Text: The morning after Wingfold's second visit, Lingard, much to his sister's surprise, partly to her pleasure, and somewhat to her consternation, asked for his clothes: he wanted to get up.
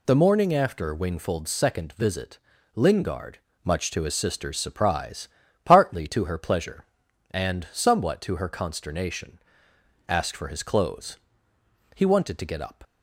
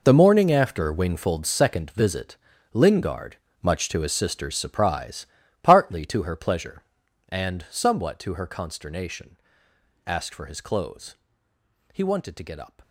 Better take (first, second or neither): first